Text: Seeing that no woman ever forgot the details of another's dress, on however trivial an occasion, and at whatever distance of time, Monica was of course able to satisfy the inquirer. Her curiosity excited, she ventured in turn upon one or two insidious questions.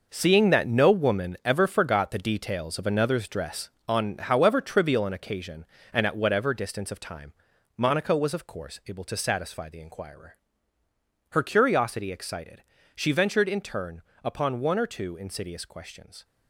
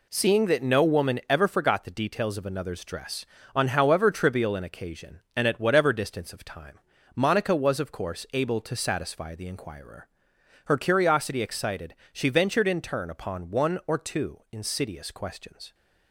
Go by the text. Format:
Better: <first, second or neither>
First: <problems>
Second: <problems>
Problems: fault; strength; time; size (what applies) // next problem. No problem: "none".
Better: second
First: gets quieter; strong; throughout; 10 dB // pauses between "turn" and "upon"; slight; at 14.0 s; 0.22 s long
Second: none